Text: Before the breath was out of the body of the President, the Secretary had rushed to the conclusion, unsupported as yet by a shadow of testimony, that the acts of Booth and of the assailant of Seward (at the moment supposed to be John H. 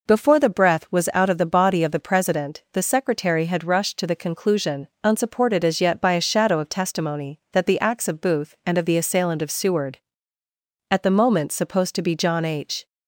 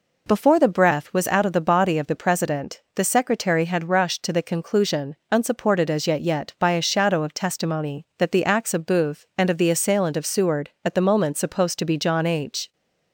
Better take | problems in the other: first | says "yet" twice; at 6.1 s

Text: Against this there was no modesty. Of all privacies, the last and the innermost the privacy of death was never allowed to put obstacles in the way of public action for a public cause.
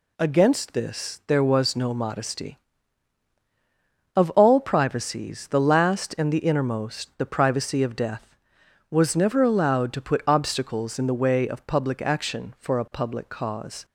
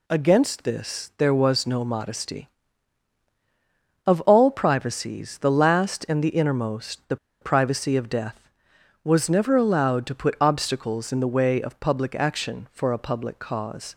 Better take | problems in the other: first | pauses between "the" and "privacy"; slight; at 7.1 s; 0.25 s long

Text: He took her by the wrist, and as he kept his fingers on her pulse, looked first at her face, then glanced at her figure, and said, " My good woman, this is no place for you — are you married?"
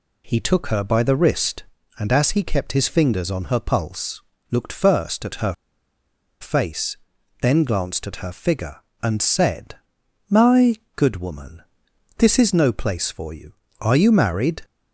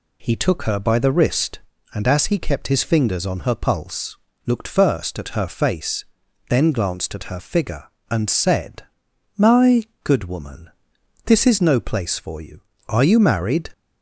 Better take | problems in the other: second | pauses between "her" and "face"; noticeable; at 5.5 s; 0.87 s long // pauses between "My" and "good"; slight; at 10.7 s; 0.20 s long; slight in the second

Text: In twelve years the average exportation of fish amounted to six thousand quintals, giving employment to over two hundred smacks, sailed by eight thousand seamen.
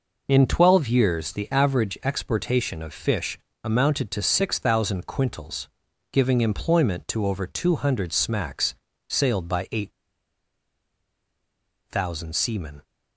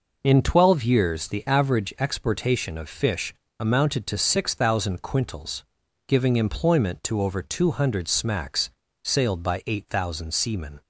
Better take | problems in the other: second | pauses between "fish" and "amounted"; slight; at 3.3 s; 0.26 s long; slight in the second // pauses between "eight" and "thousand"; strong; at 9.9 s; 1.9 s long

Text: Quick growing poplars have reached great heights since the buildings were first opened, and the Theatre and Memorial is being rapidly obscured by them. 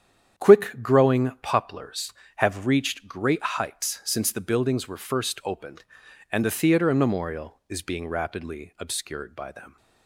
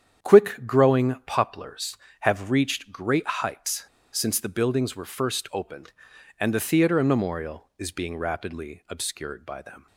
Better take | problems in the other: first | starts louder than the rest; strong; until 1.3 s; 8.5 dB; strong in the first // pauses between "heights" and "since"; slight; at 3.8 s; 0.28 s long

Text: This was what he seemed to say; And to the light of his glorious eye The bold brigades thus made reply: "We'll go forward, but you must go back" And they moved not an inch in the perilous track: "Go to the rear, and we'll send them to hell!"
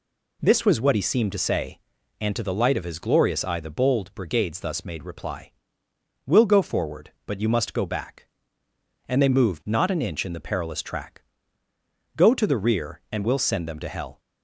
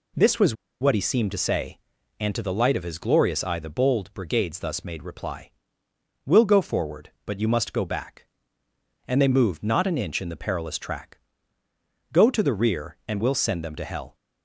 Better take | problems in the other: first | pauses between "was" and "what"; slight; at 0.5 s; 0.27 s long

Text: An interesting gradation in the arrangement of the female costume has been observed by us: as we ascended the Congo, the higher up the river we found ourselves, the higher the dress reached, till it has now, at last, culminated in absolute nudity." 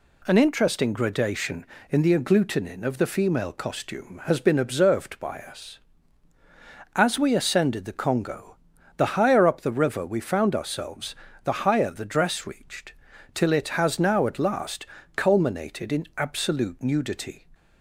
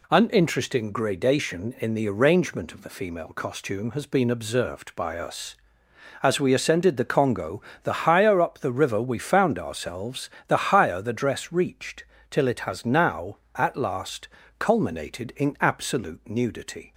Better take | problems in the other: second | says "agglutinin" for "arrangement"; at 2.1 s

